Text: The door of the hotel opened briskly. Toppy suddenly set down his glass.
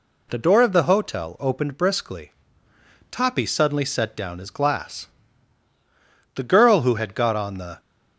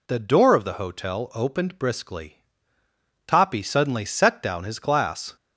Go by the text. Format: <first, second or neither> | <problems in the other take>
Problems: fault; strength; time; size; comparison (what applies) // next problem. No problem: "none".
second | goes on to say "The girl who had got on the"; from 6.3 s on; 1.4 s long